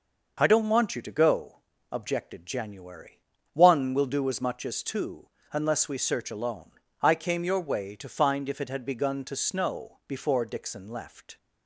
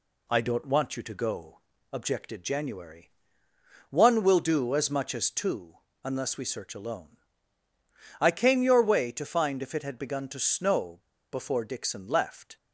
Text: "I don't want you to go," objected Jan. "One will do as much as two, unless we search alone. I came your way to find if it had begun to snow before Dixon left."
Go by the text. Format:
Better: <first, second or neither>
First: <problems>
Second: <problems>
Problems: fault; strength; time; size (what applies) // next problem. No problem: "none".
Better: first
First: none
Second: pauses between "snow" and "before"; slight; at 10.9 s; 0.31 s long